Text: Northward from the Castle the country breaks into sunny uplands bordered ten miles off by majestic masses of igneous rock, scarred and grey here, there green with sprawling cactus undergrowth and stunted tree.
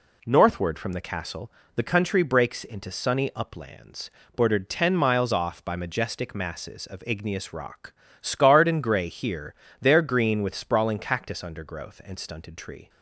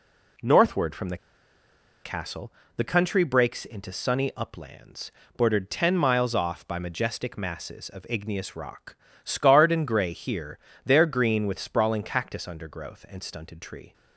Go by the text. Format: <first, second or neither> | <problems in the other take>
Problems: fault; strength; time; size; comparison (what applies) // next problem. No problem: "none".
first | pauses between "the" and "Castle"; noticeable; at 1.1 s; 0.87 s long // pauses between "Castle" and "the"; slight; at 2.5 s; 0.26 s long; slight in the first // pauses between "uplands" and "bordered"; slight; at 5.1 s; 0.26 s long; slight in the first